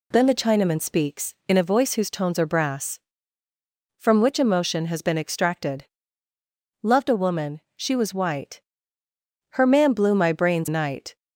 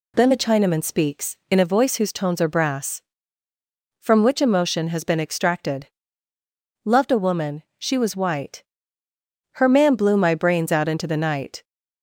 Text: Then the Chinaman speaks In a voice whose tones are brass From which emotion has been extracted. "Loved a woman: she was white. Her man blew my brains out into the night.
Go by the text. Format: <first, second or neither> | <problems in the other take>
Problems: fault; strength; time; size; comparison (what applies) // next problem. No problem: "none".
second | skips "out into the"; at 10.6 s